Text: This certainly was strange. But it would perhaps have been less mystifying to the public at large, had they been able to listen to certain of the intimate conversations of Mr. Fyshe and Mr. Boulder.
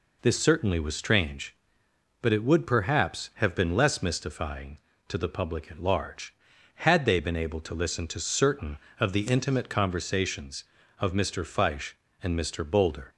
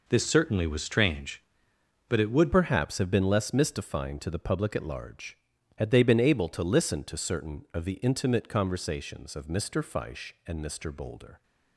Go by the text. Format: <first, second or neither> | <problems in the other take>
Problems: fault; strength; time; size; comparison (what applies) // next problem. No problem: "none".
first | changes voice at "perhaps"; from 2.5 s on; 8.9 s long